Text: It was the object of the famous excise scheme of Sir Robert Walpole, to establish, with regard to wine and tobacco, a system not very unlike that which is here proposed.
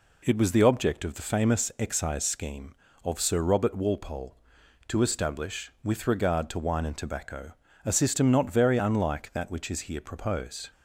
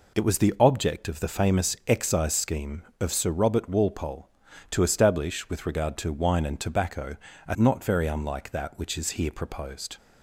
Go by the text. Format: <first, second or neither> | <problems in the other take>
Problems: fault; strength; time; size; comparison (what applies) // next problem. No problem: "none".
first | skips "system"; at 7.5 s